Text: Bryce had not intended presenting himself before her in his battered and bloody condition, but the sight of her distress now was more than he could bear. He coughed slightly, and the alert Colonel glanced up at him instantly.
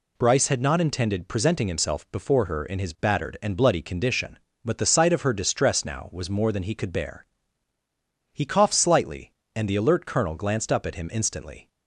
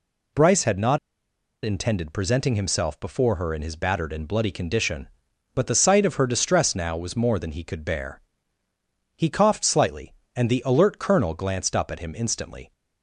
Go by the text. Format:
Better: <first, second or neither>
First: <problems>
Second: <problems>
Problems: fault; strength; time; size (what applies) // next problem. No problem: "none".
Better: first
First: none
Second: pauses between "not" and "intended"; noticeable; at 0.9 s; 0.67 s long